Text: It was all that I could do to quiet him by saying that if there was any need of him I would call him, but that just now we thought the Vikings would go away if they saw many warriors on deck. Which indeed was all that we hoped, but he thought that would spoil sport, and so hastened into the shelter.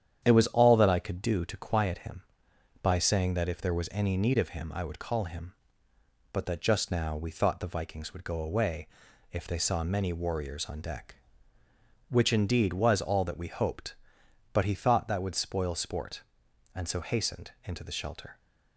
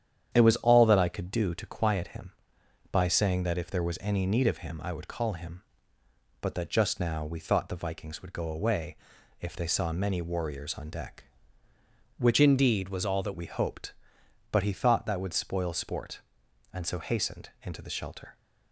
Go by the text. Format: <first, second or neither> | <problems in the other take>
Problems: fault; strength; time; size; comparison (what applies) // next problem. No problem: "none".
first | starts louder than the rest; strong; until 1.3 s; 9 dB; strong in the first // pauses between "away" and "if"; at 8.9 s; 0.44 s long; also in the first // changes voice from "indeed" to "that"; from 12.3 to 13.3 s; 1.0 s long